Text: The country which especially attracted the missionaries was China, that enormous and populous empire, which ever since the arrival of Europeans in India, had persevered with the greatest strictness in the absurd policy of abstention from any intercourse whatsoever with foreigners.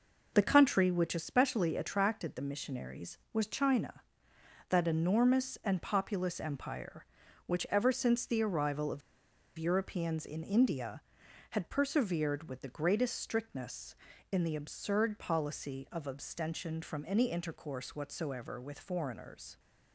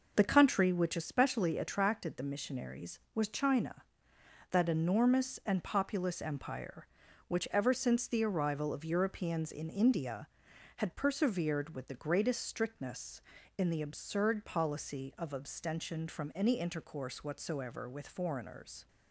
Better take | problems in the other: second | pauses between "of" and "Europeans"; noticeable; at 9.0 s; 0.58 s long

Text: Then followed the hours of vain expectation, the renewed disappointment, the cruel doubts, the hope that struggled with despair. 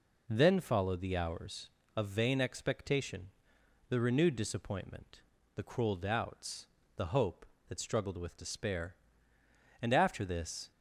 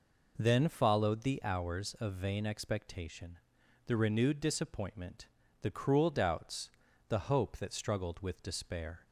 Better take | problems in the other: second | goes on to say "And after this"; noticeable; from 9.8 s on; 0.90 s long

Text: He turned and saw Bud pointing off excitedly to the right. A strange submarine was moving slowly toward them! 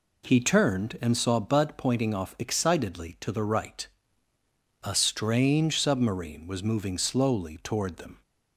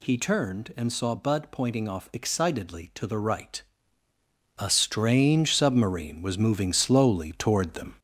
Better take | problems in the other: first | gets louder; throughout; 3.5 dB

